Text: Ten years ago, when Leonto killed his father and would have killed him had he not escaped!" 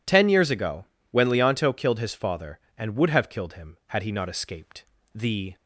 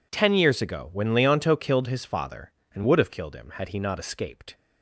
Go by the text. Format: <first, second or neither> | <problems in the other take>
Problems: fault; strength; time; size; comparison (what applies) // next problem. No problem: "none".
second | goes on to say "The"; slight; from 5.1 s on; 0.42 s long